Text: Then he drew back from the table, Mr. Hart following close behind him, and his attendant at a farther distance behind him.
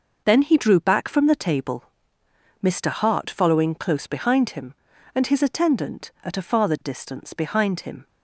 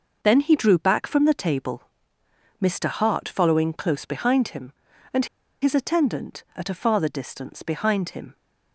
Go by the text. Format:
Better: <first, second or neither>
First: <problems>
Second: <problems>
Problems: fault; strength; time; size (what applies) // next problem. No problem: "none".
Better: first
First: none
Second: pauses between "and" and "his"; at 5.2 s; 0.36 s long